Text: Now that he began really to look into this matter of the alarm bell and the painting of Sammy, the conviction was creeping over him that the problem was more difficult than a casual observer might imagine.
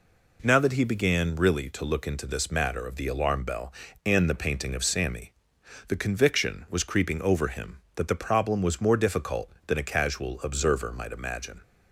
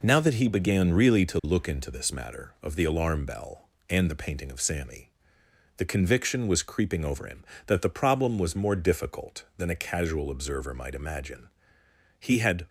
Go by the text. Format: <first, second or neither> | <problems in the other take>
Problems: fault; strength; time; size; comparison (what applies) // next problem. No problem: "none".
first | goes on to say "He had"; slight; from 12.1 s on; 0.48 s long